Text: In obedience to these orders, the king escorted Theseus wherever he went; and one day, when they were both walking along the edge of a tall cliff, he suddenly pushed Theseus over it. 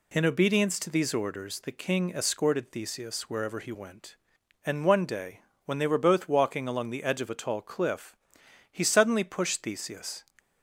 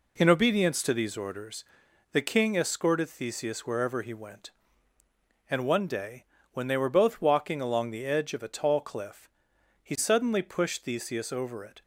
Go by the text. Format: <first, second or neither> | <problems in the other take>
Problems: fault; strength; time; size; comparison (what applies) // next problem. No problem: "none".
second | stops before "over it"; at 10.3 s